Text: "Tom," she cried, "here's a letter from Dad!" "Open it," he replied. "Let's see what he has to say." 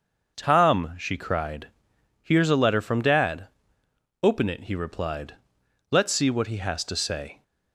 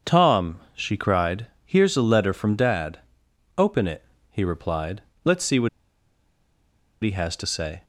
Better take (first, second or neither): first